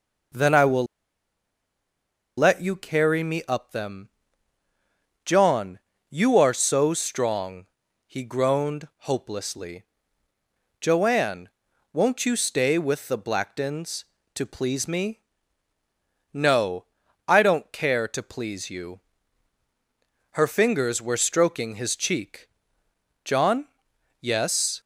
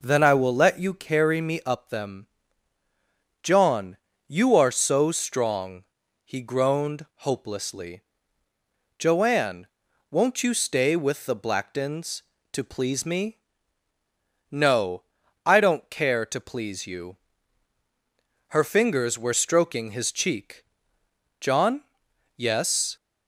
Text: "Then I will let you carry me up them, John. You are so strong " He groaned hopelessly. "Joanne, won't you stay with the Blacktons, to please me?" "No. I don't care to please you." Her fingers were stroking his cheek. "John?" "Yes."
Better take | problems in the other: second | pauses between "will" and "let"; strong; at 0.8 s; 1.5 s long

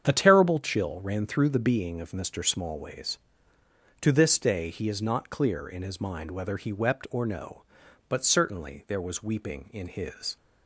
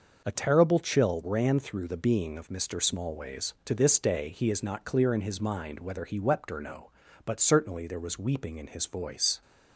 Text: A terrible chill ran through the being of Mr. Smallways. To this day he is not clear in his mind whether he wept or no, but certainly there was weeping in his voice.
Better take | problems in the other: second | starts louder than the rest; strong; until 1.0 s; 8 dB // stops before "voice"; at 10.3 s

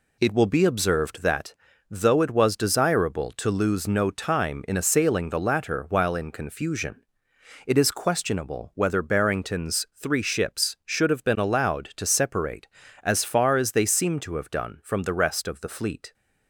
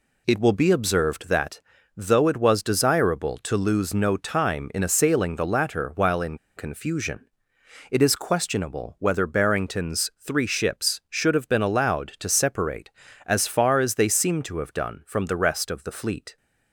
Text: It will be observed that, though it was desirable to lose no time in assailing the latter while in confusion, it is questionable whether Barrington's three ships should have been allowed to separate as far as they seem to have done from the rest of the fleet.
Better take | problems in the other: first | pauses between "in" and "confusion"; slight; at 6.3 s; 0.18 s long

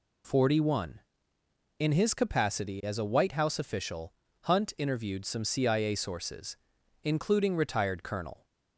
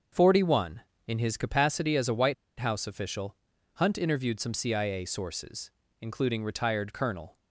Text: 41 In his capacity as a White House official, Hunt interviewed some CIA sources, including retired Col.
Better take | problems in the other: first | starts louder than the rest; until 1.4 s; 6.5 dB // pauses between "White" and "House"; slight; at 2.3 s; 0.25 s long

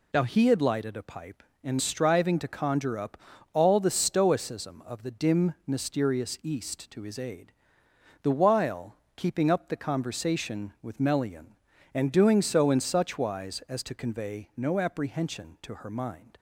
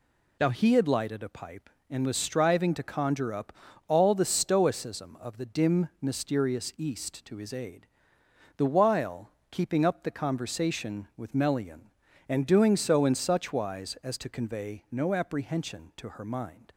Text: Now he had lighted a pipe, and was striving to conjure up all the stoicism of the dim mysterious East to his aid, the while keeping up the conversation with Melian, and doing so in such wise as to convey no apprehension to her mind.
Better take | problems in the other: second | skips "was"; at 1.7 s // pauses between "up" and "all"; slight; at 3.1 s; 0.36 s long; slight in the second // pauses between "while" and "keeping"; slight; at 8.9 s; 0.22 s long; slight in the second

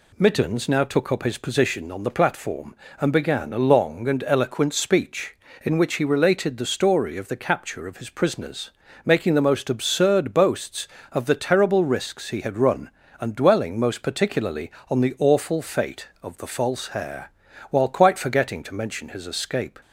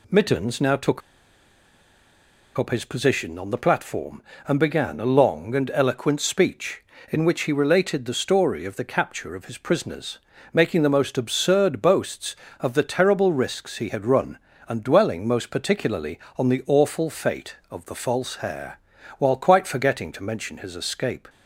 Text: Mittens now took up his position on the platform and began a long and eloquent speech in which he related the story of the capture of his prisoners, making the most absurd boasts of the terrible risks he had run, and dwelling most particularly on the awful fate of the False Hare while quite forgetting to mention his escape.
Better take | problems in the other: first | pauses between "took" and "up"; strong; at 1.0 s; 1.5 s long // pauses between "Hare" and "while"; at 18.7 s; 0.40 s long; also in the first

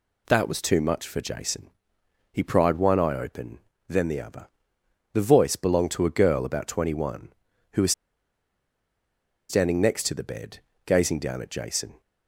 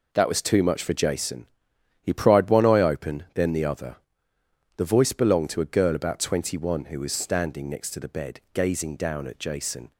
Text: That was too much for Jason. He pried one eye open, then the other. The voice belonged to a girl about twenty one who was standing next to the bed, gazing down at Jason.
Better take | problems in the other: second | pauses between "was" and "standing"; strong; at 7.9 s; 1.5 s long

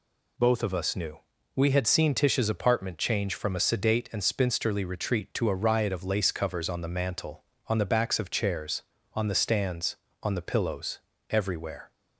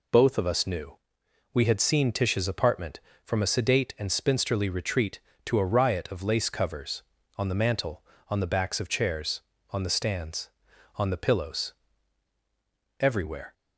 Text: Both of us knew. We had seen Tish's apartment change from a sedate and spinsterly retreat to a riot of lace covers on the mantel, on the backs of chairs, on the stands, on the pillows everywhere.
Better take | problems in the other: first | skips "change"; at 3.1 s // pauses between "pillows" and "everywhere"; strong; at 11.7 s; 1.2 s long; slight in the first

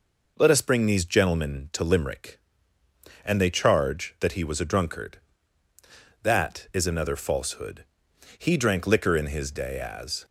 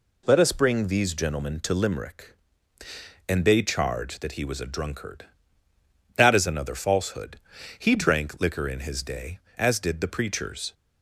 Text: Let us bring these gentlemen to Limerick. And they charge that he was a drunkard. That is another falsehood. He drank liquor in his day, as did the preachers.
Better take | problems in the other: second | stops before "did the preachers"; at 10.2 s

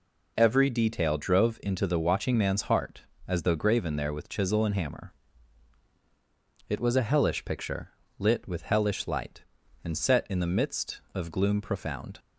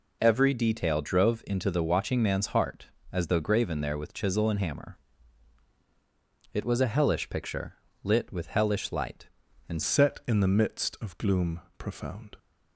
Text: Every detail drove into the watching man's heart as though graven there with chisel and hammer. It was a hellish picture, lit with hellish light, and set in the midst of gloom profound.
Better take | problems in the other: first | changes voice at "set"; from 9.8 s on; 2.5 s long // pauses between "gloom" and "profound"; slight; at 11.5 s; 0.18 s long

